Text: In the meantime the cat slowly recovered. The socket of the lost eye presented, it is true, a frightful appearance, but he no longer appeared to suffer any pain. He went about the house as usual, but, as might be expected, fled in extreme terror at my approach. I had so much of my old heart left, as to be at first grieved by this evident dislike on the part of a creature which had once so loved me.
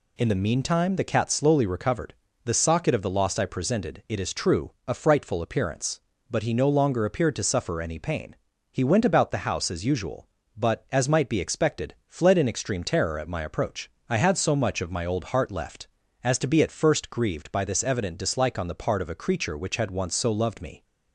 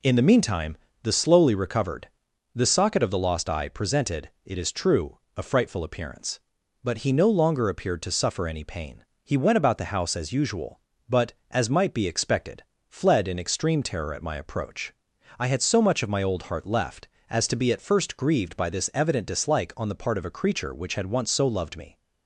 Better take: first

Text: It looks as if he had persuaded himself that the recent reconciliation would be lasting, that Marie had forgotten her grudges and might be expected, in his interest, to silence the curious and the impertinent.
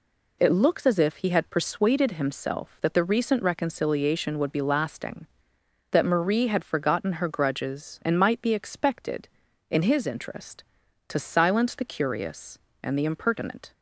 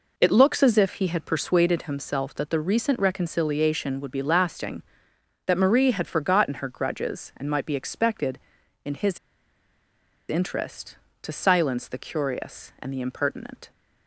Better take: first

